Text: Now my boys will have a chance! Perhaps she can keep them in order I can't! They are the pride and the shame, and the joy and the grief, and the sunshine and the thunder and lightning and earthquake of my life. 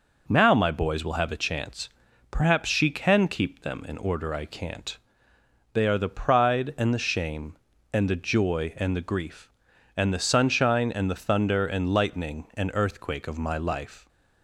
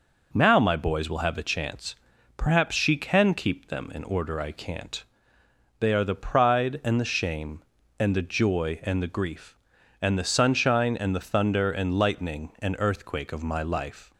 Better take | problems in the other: neither | none

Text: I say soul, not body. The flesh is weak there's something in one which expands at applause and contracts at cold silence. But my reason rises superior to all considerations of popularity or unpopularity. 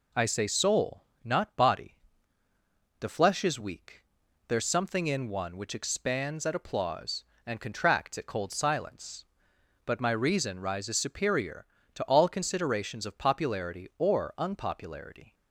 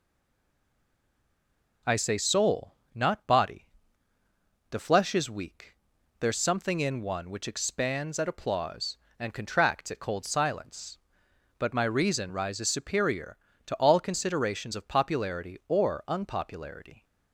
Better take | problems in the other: first | stays silent before the first word; noticeable; until 1.8 s; 1.8 s long // pauses between "weak" and "there's"; noticeable; at 5.7 s; 0.46 s long; noticeable in the first

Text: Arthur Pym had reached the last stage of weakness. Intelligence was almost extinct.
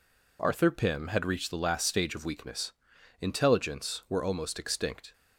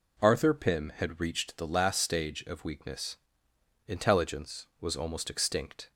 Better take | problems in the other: second | says "were" for "was"; at 4.0 s

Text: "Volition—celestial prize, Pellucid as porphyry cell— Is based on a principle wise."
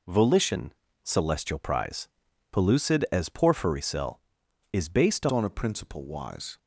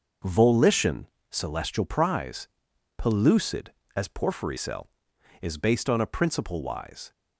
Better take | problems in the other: second | changes voice at "on"; from 5.3 s on; 1.2 s long

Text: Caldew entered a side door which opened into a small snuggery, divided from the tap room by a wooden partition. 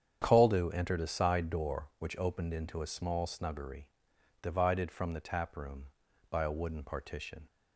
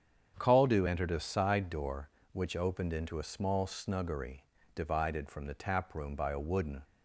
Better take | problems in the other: first | starts louder than the rest; strong; until 1.3 s; 8 dB; strong in the first // stops before "partition"; at 6.8 s

